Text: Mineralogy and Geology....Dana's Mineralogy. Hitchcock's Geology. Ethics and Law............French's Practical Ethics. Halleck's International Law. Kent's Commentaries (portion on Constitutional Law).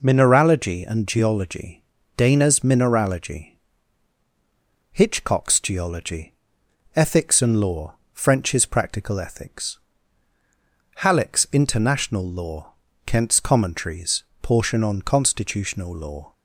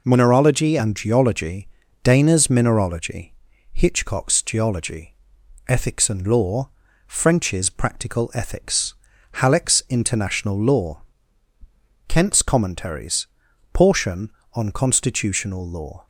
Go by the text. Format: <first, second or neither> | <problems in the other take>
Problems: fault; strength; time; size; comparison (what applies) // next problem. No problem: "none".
neither | none